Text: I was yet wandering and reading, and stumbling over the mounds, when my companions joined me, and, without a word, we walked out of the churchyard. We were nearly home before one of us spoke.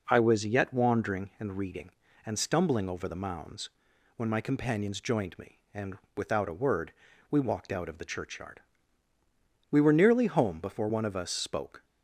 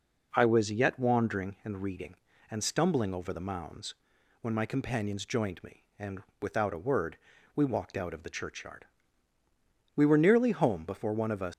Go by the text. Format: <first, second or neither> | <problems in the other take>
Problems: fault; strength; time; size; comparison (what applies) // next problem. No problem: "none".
first | stops before "spoke"; at 11.5 s